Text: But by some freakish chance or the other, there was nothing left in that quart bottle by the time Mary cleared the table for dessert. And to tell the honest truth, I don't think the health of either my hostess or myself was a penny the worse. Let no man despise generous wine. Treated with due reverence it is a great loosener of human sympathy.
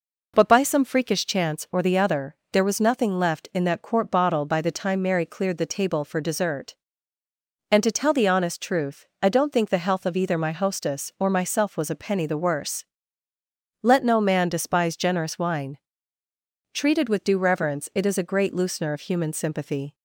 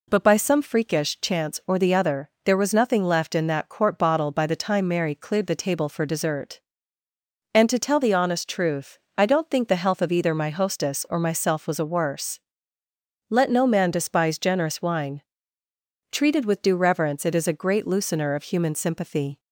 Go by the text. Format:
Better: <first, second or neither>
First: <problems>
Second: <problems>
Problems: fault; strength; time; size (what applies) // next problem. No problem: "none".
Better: first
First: none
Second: skips "penny the"; at 11.8 s